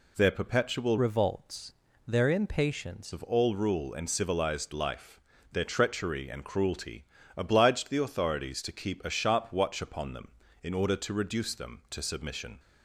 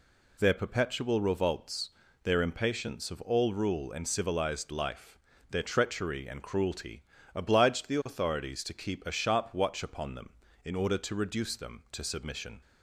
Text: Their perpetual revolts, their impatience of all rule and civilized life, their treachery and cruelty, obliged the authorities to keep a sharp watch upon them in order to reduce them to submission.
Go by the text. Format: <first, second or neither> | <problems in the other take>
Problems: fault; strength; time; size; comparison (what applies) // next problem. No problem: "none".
second | changes voice from "revolts" to "impatience"; from 0.9 to 3.1 s; 2.2 s long